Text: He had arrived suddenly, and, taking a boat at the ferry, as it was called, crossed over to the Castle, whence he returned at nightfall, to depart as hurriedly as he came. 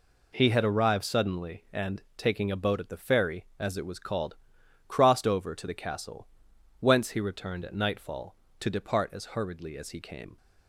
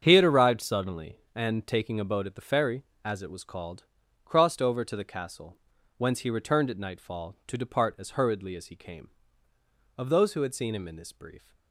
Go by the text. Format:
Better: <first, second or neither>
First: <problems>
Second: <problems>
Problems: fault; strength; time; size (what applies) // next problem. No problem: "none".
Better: first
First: none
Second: starts louder than the rest; strong; until 1.0 s; 7.5 dB // goes on to say "Of those who had seen him in this brief"; from 9.9 s on; 1.5 s long